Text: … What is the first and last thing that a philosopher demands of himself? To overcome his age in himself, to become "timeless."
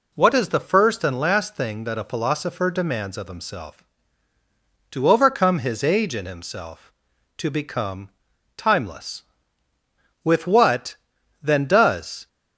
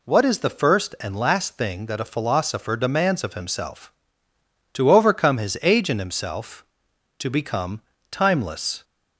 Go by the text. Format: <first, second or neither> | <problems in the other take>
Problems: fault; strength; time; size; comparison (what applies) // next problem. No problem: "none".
second | pauses between "become" and "timeless"; noticeable; at 8.0 s; 0.46 s long; slight in the second // goes on to say "With what then does"; strong; from 10.2 s on; 2.0 s long